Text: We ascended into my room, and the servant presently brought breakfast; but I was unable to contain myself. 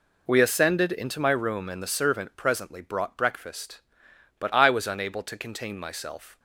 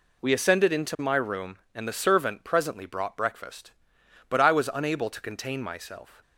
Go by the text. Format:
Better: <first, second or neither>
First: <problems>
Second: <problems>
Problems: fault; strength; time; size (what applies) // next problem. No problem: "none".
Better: neither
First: none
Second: none